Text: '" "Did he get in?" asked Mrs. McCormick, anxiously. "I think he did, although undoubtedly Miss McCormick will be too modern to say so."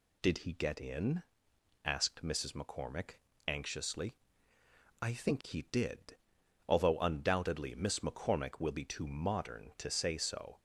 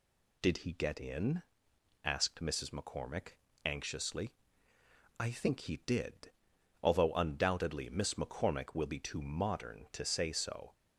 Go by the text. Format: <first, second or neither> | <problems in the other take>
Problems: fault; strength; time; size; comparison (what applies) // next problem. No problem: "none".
neither | none